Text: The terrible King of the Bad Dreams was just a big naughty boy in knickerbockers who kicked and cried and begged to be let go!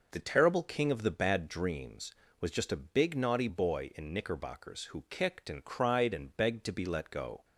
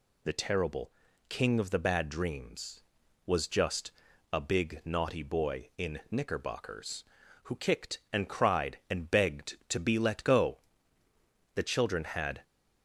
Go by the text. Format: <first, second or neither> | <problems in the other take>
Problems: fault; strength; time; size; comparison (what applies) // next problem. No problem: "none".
first | pauses between "terrible" and "King"; at 0.9 s; 0.38 s long // pauses between "just" and "a"; at 3.9 s; 0.40 s long // goes on to say "The children had"; noticeable; from 11.5 s on; 0.88 s long